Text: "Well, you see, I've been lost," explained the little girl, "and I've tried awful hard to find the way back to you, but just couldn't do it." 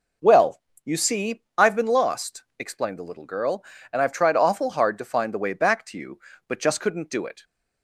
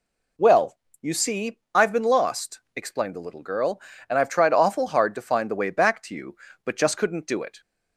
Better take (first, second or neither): second